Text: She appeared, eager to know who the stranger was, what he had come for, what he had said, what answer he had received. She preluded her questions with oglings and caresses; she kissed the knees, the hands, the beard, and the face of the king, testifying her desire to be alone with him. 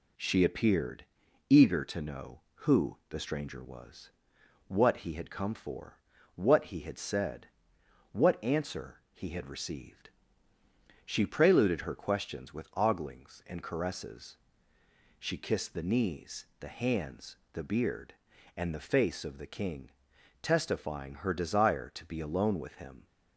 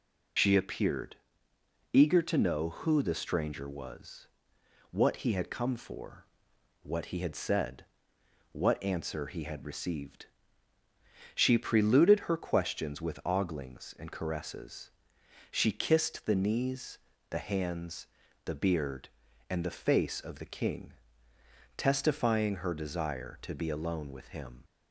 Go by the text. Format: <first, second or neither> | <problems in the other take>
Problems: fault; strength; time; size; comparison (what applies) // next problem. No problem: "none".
first | loses the start of "She"; at 0.3 s; 35 ms